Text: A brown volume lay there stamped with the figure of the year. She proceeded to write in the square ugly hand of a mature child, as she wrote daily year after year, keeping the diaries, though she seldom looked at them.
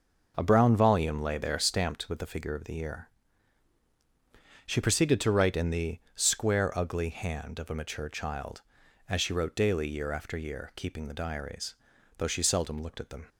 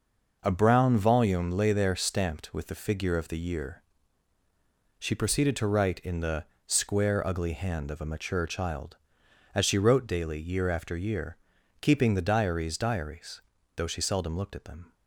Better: first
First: none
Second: pauses between "the" and "square"; slight; at 6.4 s; 0.20 s long // says "diaries" twice; at 12.7 s

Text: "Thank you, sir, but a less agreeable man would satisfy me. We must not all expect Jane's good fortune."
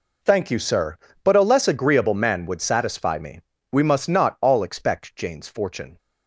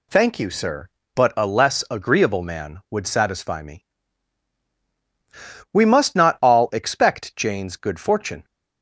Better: second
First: skips "good"; at 5.4 s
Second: none

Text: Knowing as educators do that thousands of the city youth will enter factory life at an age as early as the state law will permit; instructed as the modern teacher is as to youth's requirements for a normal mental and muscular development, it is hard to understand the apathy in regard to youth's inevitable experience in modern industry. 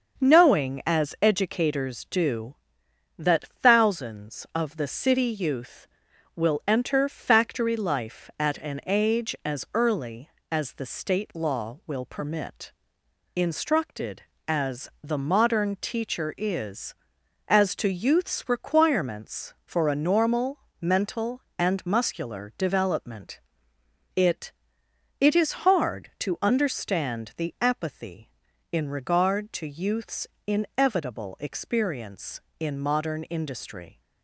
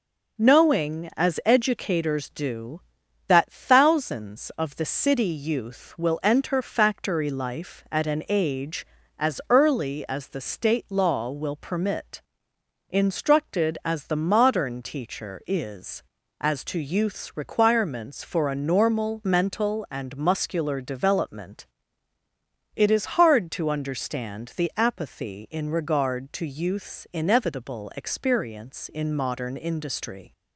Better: second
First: starts louder than the rest; until 1.3 s; 6.5 dB // pauses between "normal" and "mental"; slight; at 20.5 s; 0.24 s long // says "it" twice; at 25.2 s // pauses between "youth's" and "inevitable"; slight; at 30.2 s; 0.18 s long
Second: none

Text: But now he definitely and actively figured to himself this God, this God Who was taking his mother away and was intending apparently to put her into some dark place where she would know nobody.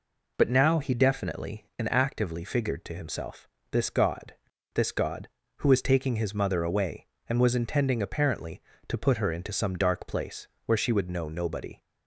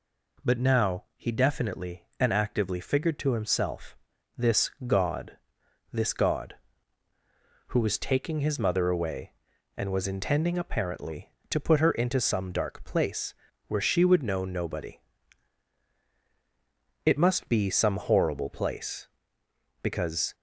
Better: first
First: pauses between "himself" and "this"; slight; at 3.4 s; 0.24 s long // pauses between "place" and "where"; slight; at 10.4 s; 0.18 s long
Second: pauses between "himself" and "this"; at 3.9 s; 0.40 s long // pauses between "this" and "God"; slight; at 4.7 s; 0.16 s long // pauses between "place" and "where"; slight; at 13.3 s; 0.34 s long // goes on to say "It must be some horrible place because"; strong; from 17.0 s on; 3.3 s long

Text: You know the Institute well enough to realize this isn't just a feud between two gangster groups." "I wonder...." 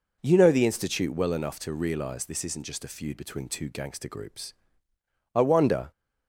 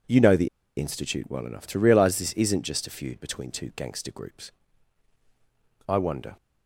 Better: first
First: none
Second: pauses between "the" and "Institute"; slight; at 0.4 s; 0.29 s long

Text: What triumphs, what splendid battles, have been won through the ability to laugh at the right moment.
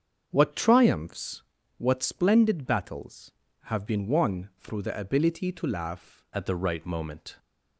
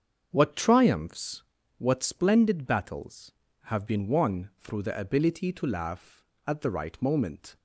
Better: second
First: starts louder than the rest; strong; until 1.3 s; 7 dB // changes voice at "at"; from 6.3 s on; 1.0 s long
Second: starts louder than the rest; until 1.3 s; 7 dB

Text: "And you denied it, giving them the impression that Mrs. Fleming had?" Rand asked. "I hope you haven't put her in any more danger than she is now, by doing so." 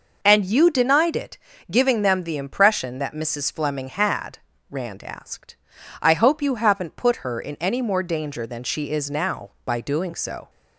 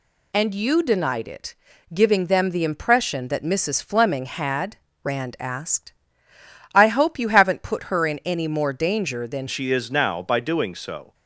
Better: first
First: none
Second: changes voice at "she"; from 9.4 s on; 1.7 s long

